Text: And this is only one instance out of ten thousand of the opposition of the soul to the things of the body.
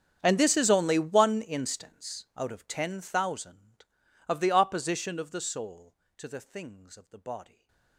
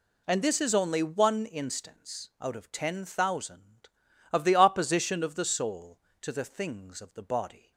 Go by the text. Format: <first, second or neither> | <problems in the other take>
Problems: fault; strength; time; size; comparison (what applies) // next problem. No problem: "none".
second | gets quieter; strong; throughout; 23.5 dB // stays silent after the last word; slight; from 7.4 s on; 0.5 s long